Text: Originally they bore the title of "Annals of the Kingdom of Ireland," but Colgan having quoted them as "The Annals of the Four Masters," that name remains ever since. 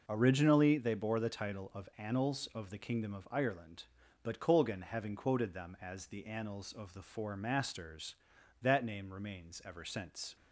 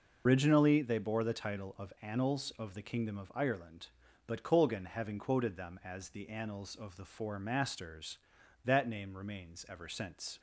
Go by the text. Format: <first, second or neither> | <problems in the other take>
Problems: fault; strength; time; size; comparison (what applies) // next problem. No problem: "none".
first | loses the start of "Originally"; at 0.2 s; 130 ms